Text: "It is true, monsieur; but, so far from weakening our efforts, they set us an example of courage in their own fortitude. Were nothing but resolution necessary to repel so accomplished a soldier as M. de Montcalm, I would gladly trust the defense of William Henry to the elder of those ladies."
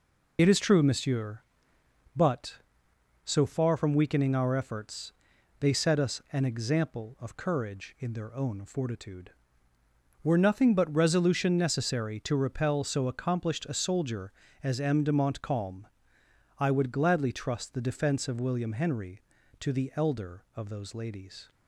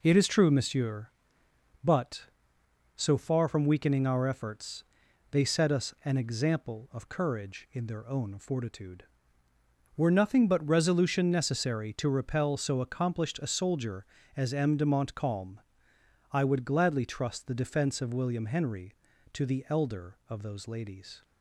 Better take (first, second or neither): second